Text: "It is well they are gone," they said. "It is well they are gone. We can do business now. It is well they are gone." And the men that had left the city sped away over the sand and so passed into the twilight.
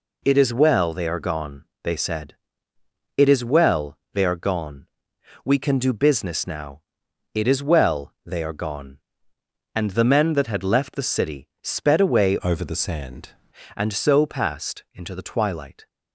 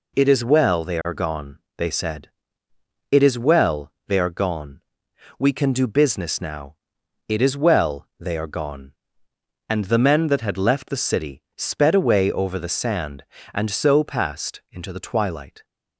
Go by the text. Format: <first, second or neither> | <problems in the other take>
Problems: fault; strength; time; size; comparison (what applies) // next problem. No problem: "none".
second | changes voice from "over" to "sand"; from 12.4 to 13.2 s; 0.8 s long